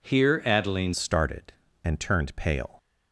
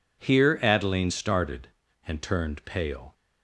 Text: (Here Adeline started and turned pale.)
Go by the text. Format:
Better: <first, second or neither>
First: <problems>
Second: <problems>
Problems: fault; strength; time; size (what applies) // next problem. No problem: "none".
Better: second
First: changes voice at "started"; from 0.9 s on; 1.8 s long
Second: none